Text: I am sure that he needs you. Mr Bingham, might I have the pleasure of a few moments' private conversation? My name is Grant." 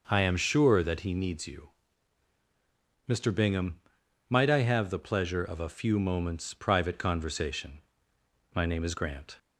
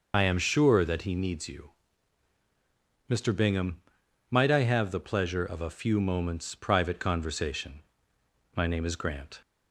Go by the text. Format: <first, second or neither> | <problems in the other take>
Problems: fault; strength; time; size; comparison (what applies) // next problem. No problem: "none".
first | loses the start of "I"; at 0.1 s; 65 ms